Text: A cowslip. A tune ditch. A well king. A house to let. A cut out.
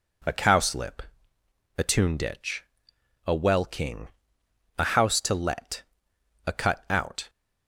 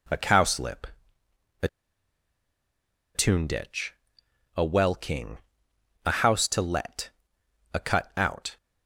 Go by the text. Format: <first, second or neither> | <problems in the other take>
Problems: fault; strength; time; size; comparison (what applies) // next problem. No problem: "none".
first | pauses between "A" and "tune"; strong; at 1.6 s; 1.4 s long